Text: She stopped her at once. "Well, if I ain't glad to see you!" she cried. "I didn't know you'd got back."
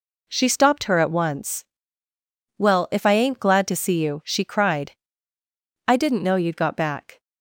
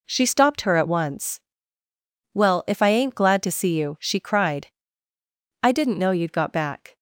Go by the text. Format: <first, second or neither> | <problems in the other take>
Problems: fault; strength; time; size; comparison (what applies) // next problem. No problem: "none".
neither | none